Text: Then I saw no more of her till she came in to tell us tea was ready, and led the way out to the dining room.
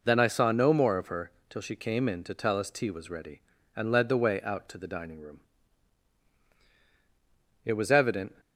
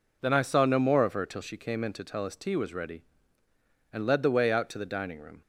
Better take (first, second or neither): second